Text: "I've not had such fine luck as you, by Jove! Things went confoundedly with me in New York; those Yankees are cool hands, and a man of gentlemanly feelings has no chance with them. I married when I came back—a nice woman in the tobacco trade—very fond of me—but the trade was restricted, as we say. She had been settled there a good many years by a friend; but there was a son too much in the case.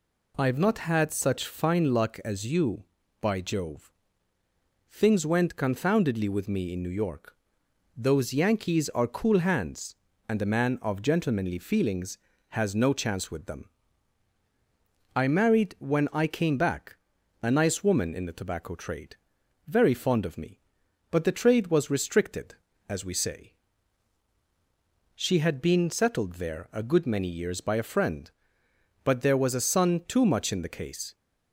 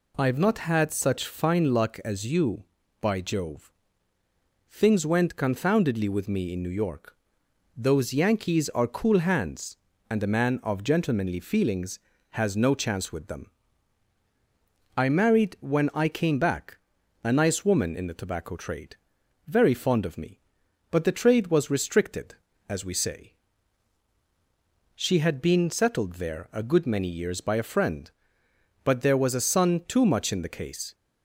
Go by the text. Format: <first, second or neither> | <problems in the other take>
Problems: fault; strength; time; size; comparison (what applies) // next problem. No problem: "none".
neither | none